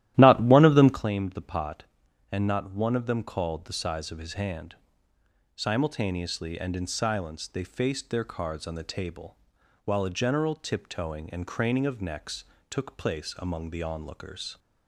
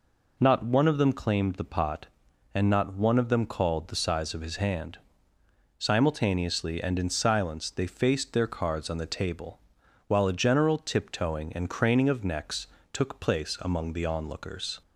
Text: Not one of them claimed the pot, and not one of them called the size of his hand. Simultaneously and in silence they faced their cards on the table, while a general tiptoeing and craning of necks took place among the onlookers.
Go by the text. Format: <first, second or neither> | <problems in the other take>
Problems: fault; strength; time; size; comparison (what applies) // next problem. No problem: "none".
second | starts louder than the rest; strong; until 1.1 s; 13.5 dB // pauses between "necks" and "took"; slight; at 12.4 s; 0.24 s long; slight in the second